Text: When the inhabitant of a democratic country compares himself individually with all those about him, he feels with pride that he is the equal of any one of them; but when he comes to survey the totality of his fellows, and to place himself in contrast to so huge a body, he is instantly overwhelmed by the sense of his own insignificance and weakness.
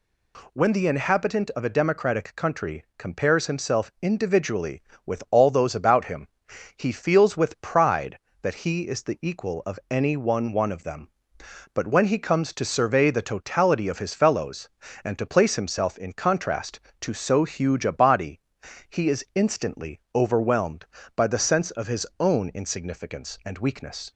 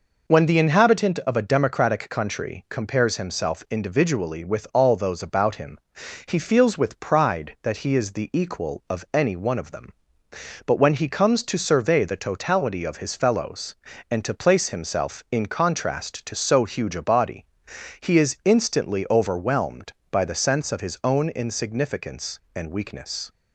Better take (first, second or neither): second